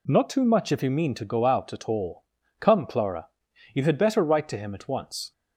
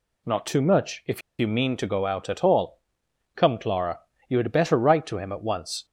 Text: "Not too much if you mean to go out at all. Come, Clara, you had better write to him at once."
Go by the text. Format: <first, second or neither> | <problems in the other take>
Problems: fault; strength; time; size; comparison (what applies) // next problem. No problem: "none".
first | pauses between "if" and "you"; slight; at 1.2 s; 0.18 s long